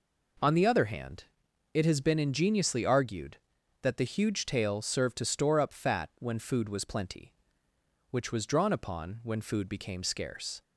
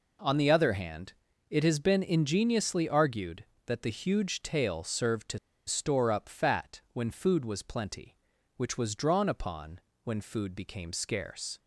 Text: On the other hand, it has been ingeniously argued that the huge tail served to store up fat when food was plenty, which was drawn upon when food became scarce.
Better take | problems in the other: first | pauses between "to" and "store"; slight; at 5.3 s; 0.28 s long // pauses between "upon" and "when"; slight; at 9.7 s; 0.26 s long

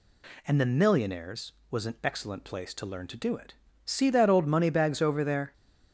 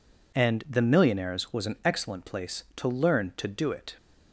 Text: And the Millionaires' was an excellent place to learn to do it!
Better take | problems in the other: second | goes on to say "See that old money bags over there"; strong; from 3.8 s on; 1.6 s long

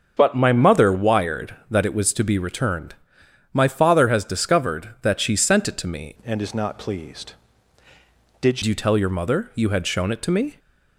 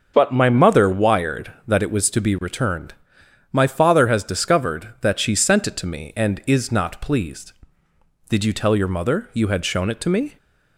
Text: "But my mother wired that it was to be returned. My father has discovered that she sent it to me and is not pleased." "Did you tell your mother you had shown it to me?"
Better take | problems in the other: second | starts louder than the rest; until 1.1 s; 6.5 dB; also in the second // changes voice from "and" to "Did"; from 6.2 to 8.6 s; 2.4 s long

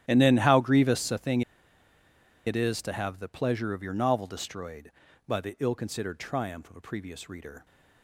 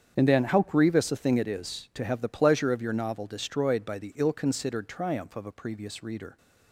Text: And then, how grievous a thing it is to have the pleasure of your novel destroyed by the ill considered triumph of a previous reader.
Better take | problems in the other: second | starts louder than the rest; strong; until 1.0 s; 12 dB; strong in the second // pauses between "thing" and "it"; at 1.4 s; 1.0 s long

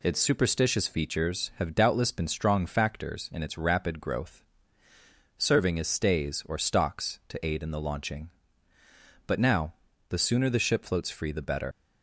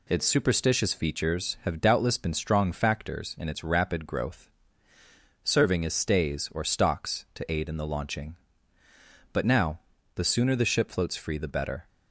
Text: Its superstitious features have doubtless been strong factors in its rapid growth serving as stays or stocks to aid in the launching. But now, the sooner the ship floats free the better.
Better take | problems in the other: second | pauses between "growth" and "serving"; noticeable; at 4.4 s; 0.94 s long; noticeable in the second // leaves "better" unfinished; at 11.7 s; 105 ms

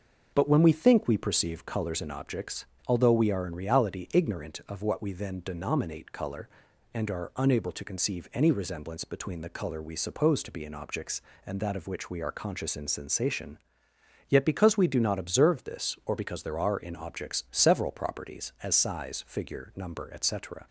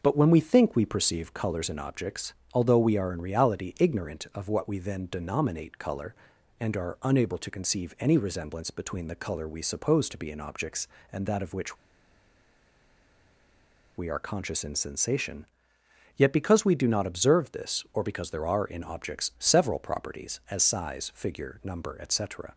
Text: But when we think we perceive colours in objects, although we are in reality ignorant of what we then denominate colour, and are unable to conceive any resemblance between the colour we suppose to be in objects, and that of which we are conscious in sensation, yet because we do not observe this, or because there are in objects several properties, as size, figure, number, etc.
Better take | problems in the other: first | starts louder than the rest; until 1.0 s; 6.5 dB; also in the first // pauses between "which" and "we"; strong; at 11.7 s; 2.2 s long

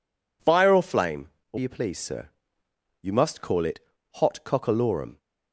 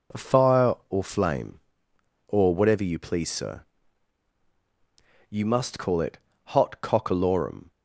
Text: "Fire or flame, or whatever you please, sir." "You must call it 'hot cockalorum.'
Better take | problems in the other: second | skips "whatever"; at 1.5 s // pauses between "it" and "hot"; slight; at 3.7 s; 0.36 s long; slight in the second

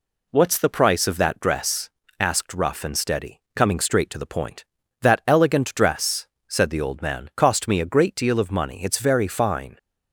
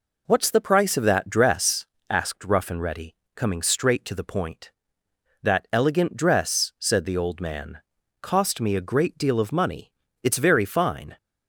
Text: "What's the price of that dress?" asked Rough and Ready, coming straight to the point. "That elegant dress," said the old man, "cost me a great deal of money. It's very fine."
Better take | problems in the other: second | says "Steady" for "Ready"; at 2.9 s

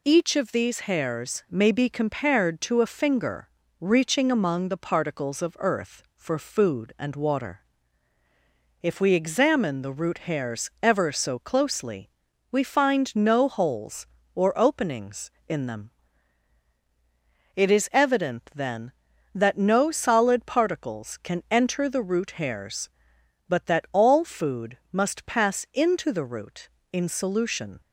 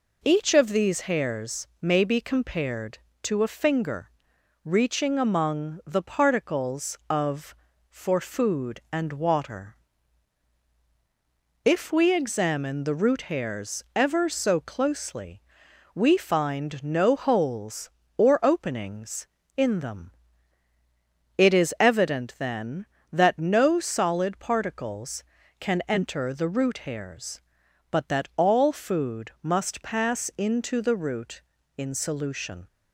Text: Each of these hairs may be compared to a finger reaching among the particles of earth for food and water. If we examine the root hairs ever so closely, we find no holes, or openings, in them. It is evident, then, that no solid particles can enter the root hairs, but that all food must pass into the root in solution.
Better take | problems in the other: first | pauses between "finger" and "reaching"; noticeable; at 4.1 s; 0.54 s long; slight in the first // skips "earth"; at 7.7 s

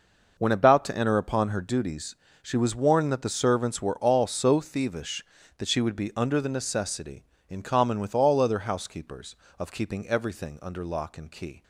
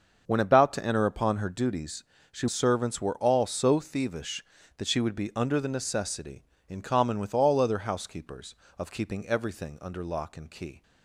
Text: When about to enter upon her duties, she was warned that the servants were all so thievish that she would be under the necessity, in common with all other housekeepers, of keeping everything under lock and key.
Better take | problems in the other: first | starts louder than the rest; until 1.2 s; 6.5 dB // skips "was warned that the"; at 2.4 s

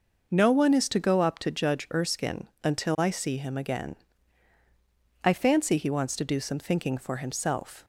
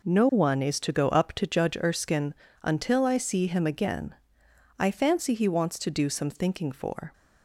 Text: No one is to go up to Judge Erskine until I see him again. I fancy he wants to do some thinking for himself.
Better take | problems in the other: first | pauses between "Erskine" and "until"; slight; at 2.3 s; 0.30 s long; slight in the first // stops before "himself"; at 7.1 s

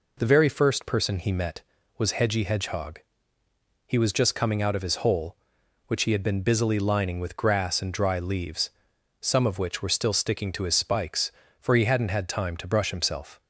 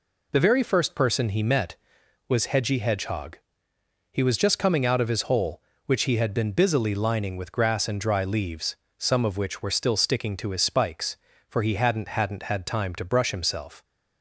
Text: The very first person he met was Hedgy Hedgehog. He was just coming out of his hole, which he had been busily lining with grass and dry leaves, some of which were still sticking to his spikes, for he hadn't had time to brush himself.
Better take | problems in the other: first | says "hadn't" twice; at 12.0 s

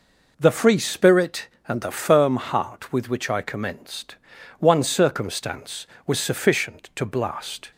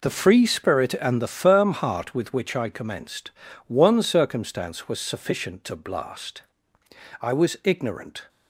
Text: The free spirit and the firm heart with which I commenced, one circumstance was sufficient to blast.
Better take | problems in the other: first | goes on to say "I was ignorant"; noticeable; from 7.2 s on; 1.0 s long

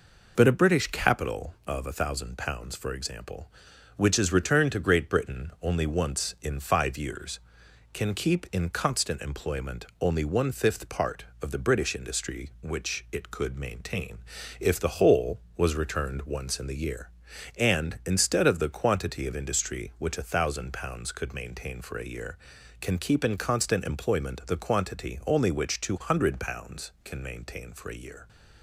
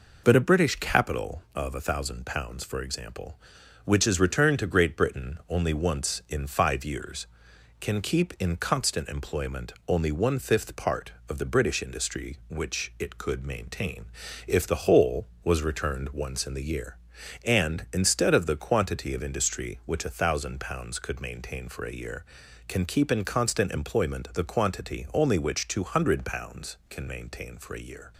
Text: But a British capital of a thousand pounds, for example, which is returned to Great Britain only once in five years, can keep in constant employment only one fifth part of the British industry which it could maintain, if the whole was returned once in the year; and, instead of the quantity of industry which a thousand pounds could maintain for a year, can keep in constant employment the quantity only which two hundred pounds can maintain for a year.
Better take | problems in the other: neither | none

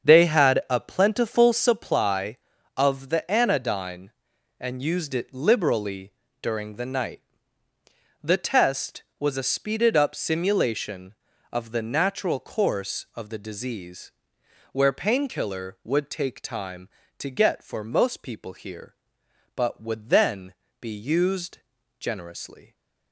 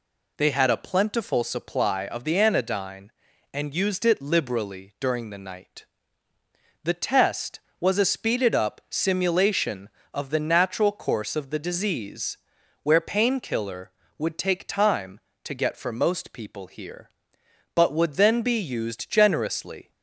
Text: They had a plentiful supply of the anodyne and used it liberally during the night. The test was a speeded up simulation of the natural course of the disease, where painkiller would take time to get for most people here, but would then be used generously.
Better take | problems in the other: second | starts louder than the rest; strong; until 1.8 s; 7.5 dB // pauses between "liberally" and "during"; slight; at 6.1 s; 0.30 s long // pauses between "then" and "be"; slight; at 20.5 s; 0.28 s long // pauses between "used" and "generously"; at 21.5 s; 0.42 s long

